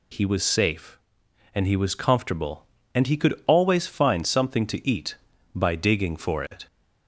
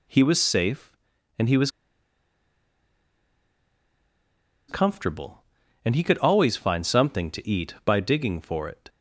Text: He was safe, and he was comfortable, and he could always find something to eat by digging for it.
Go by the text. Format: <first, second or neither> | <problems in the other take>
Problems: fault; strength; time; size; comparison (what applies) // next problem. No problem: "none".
first | pauses between "was" and "comfortable"; strong; at 1.6 s; 2.9 s long